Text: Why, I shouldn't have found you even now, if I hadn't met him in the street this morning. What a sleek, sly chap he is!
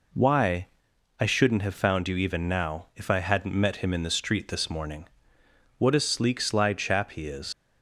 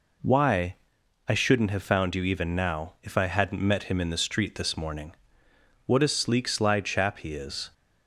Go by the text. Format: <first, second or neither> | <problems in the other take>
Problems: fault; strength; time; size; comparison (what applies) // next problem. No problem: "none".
second | leaves "is" unfinished; at 7.5 s; 130 ms